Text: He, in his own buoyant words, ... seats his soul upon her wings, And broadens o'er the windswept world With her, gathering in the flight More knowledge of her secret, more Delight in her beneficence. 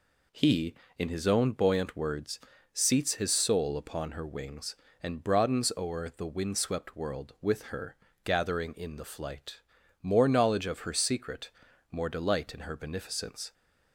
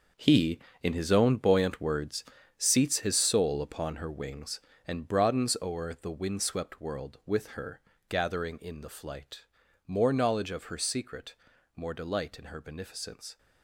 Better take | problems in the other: first | gets quieter; strong; throughout; 11 dB // pauses between "flight" and "More"; at 9.4 s; 0.42 s long; also in the first

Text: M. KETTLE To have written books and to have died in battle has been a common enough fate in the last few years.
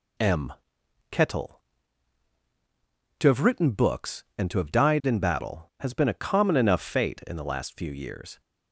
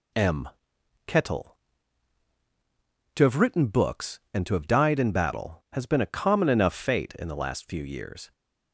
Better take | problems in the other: neither | none

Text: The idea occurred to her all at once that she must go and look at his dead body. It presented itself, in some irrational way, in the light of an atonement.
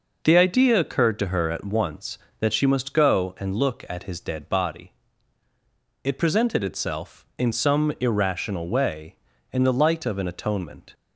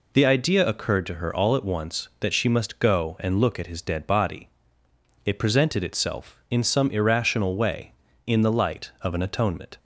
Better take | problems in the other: second | skips "all"; at 1.5 s

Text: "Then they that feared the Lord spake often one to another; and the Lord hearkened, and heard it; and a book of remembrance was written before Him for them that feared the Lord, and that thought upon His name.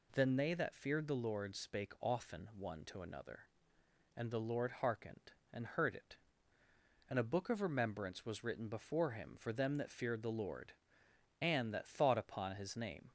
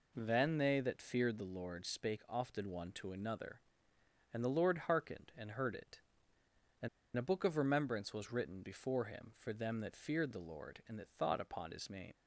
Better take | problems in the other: first | pauses between "and" and "a"; slight; at 6.8 s; 0.28 s long

